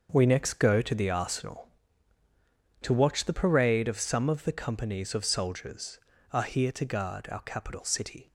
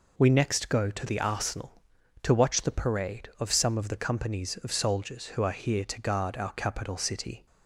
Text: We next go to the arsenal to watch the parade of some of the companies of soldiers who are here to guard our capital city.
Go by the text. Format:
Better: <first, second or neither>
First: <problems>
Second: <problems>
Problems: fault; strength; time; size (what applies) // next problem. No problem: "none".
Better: second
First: starts louder than the rest; until 1.1 s; 6.5 dB // skips "who"; at 6.1 s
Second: none